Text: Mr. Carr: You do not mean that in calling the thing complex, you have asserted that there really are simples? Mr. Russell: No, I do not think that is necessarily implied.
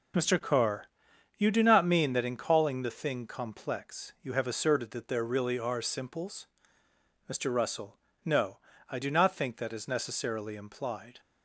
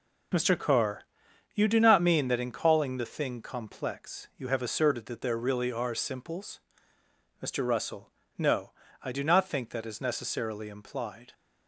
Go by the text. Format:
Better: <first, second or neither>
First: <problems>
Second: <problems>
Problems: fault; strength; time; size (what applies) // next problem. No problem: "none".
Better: neither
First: none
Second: none